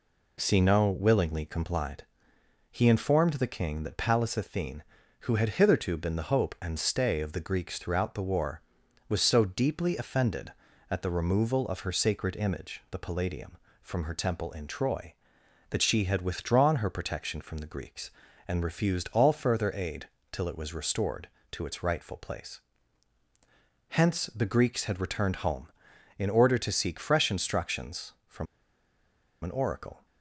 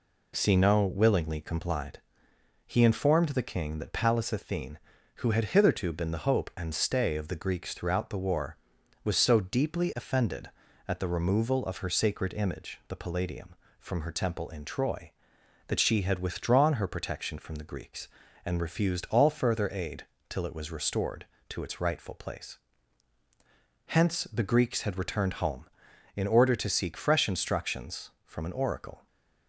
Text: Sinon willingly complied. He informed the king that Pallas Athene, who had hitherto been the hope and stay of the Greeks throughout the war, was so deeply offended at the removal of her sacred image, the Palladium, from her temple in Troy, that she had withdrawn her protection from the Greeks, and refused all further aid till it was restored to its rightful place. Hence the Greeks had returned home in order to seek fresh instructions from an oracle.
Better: second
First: pauses between "aid" and "till"; slight; at 20.0 s; 0.24 s long // pauses between "from" and "an"; noticeable; at 28.4 s; 0.97 s long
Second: pauses between "aid" and "till"; slight; at 20.0 s; 0.24 s long

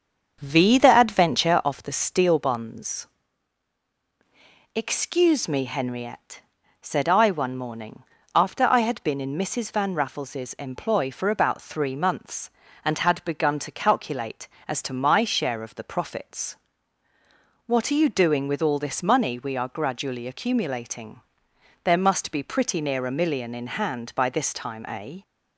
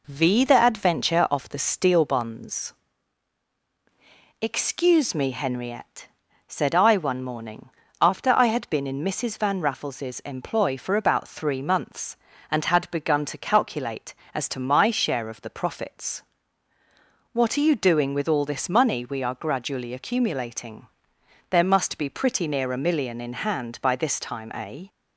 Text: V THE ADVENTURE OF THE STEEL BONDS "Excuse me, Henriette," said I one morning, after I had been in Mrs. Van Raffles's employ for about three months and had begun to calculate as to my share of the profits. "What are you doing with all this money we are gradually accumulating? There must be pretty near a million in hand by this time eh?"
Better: second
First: starts louder than the rest; strong; until 1.6 s; 7 dB // pauses between "BONDS" and "Excuse"; strong; at 3.0 s; 1.6 s long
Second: pauses between "BONDS" and "Excuse"; strong; at 2.7 s; 1.6 s long

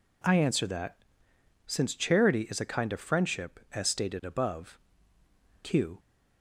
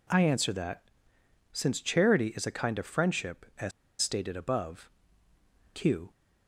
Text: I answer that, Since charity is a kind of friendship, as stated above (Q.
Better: first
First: none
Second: pauses between "as" and "stated"; slight; at 3.7 s; 0.30 s long

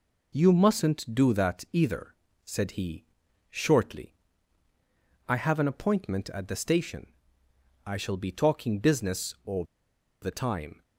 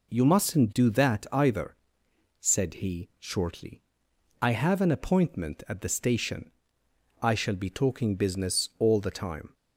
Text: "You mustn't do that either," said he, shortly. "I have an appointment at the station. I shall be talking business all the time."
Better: second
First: pauses between "all" and "the"; noticeable; at 9.6 s; 0.58 s long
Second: none

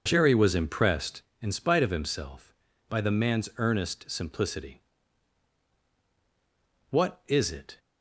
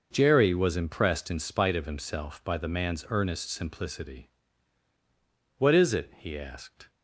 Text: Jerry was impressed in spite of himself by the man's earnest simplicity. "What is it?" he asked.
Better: second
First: stops before "he asked"; at 7.7 s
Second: none

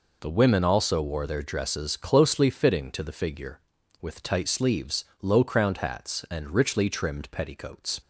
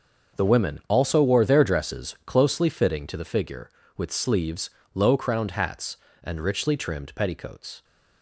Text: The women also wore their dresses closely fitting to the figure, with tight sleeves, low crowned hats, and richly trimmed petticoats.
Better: first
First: none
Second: starts louder than the rest; until 1.4 s; 6.5 dB // skips "tight"; at 4.1 s

